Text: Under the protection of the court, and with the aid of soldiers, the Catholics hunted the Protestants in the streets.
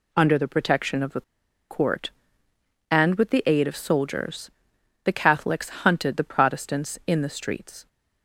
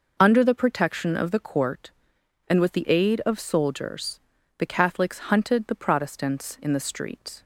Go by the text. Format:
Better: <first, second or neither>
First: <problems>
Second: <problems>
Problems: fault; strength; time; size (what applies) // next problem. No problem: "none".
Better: second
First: pauses between "the" and "court"; noticeable; at 1.2 s; 0.48 s long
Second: none